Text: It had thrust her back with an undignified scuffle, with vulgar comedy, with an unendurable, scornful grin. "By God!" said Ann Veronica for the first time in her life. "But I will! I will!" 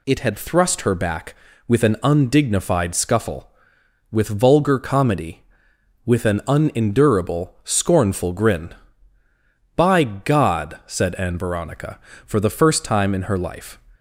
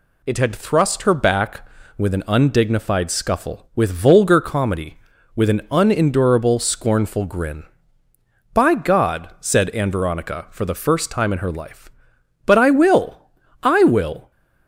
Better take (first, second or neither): second